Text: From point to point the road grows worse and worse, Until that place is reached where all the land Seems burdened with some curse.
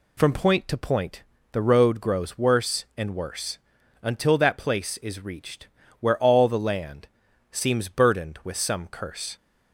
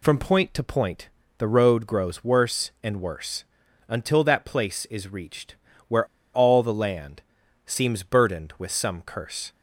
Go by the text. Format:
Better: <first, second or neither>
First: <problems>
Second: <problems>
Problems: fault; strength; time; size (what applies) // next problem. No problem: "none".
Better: first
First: pauses between "point" and "the"; slight; at 1.2 s; 0.30 s long // pauses between "reached" and "where"; slight; at 5.6 s; 0.32 s long // pauses between "land" and "Seems"; at 7.0 s; 0.44 s long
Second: pauses between "point" and "the"; slight; at 1.0 s; 0.30 s long // pauses between "reached" and "where"; slight; at 5.5 s; 0.32 s long // pauses between "where" and "all"; slight; at 6.0 s; 0.28 s long // pauses between "land" and "Seems"; at 7.2 s; 0.44 s long